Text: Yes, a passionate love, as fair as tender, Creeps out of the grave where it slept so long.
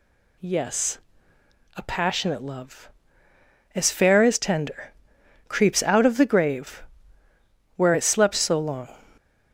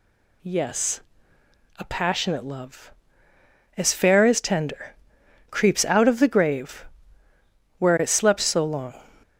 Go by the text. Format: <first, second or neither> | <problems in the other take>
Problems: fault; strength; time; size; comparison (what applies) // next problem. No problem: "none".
neither | pauses between "grave" and "where"; noticeable; the same in both